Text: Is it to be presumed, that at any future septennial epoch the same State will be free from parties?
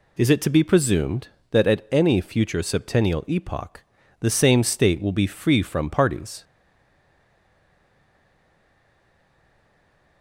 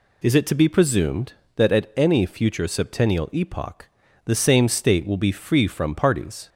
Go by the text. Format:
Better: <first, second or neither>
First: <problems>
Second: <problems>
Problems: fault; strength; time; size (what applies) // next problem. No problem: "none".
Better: second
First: pauses between "epoch" and "the"; slight; at 3.8 s; 0.36 s long // stays silent after the last word; strong; from 6.4 s on; 3.8 s long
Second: pauses between "epoch" and "the"; slight; at 3.8 s; 0.36 s long